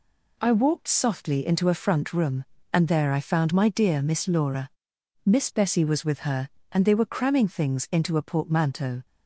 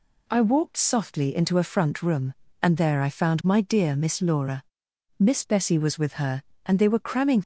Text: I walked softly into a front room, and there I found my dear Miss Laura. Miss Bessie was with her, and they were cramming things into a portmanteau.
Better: first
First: none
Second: stops before "things into a portmanteau"; at 7.4 s

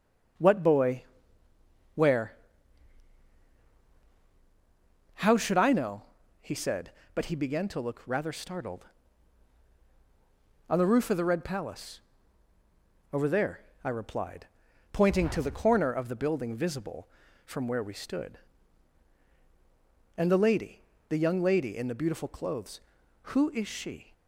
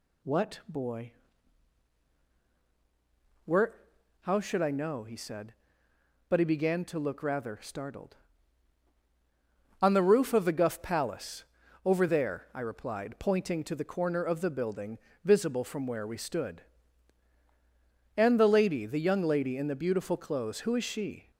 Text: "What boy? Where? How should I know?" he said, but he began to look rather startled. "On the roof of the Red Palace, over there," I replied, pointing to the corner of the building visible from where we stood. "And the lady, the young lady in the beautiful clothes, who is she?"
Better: first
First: none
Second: says "Guff" for "Red"; at 10.5 s // pauses between "building" and "visible"; slight; at 15.0 s; 0.24 s long

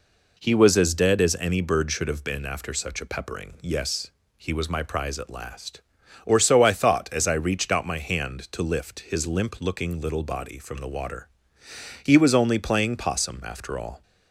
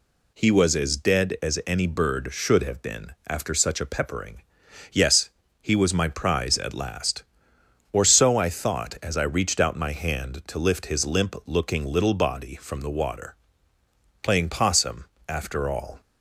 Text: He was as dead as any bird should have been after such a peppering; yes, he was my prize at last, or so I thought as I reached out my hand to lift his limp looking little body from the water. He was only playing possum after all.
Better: first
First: none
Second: pauses between "been" and "after"; slight; at 3.1 s; 0.16 s long // skips "He was only"; at 13.7 s // pauses between "possum" and "after"; slight; at 15.0 s; 0.24 s long

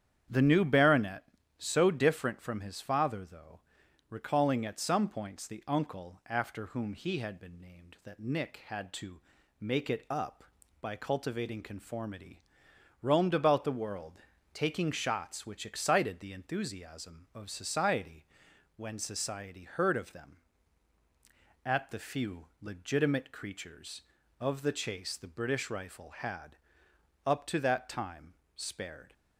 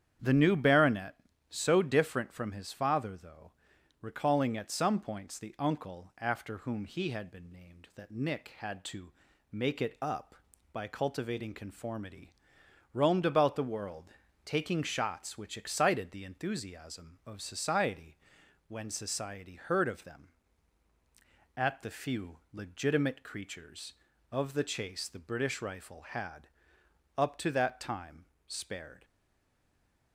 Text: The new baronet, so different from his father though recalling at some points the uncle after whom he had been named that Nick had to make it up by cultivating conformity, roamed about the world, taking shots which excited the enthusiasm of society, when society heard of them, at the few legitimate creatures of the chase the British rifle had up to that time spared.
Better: first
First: starts louder than the rest; strong; until 1.6 s; 9 dB // pauses between "though" and "recalling"; noticeable; at 3.6 s; 0.50 s long // pauses between "to" and "make"; at 9.2 s; 0.40 s long // pauses between "few" and "legitimate"; slight; at 22.4 s; 0.18 s long // pauses between "had" and "up"; noticeable; at 26.5 s; 0.70 s long // pauses between "time" and "spared"; slight; at 28.3 s; 0.22 s long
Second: starts louder than the rest; strong; until 1.5 s; 9 dB // pauses between "though" and "recalling"; noticeable; at 3.5 s; 0.50 s long // pauses between "to" and "make"; at 9.1 s; 0.40 s long // pauses between "few" and "legitimate"; slight; at 22.3 s; 0.18 s long // pauses between "had" and "up"; noticeable; at 26.4 s; 0.70 s long // pauses between "time" and "spared"; slight; at 28.2 s; 0.22 s long // stays silent after the last word; from 29.0 s on; 1.1 s long

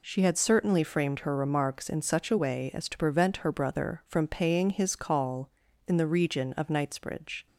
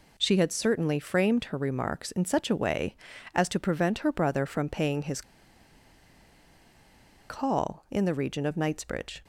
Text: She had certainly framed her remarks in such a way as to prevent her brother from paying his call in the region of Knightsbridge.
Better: first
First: none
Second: pauses between "his" and "call"; strong; at 5.2 s; 2.0 s long

